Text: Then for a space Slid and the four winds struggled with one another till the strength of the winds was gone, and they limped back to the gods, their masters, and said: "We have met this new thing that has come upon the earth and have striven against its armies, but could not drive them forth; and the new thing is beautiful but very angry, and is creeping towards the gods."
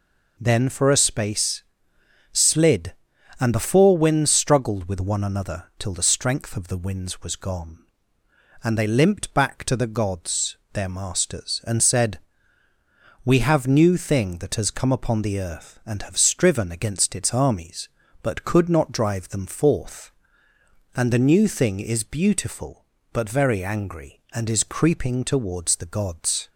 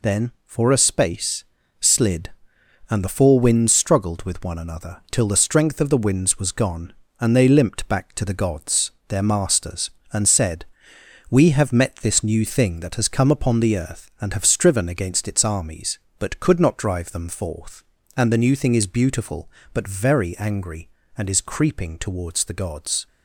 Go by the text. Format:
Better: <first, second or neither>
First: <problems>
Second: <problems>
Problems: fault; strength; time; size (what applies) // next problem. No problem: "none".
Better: second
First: pauses between "space" and "Slid"; noticeable; at 1.6 s; 0.70 s long // skips "met this"; at 13.6 s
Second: pauses between "space" and "Slid"; slight; at 1.4 s; 0.36 s long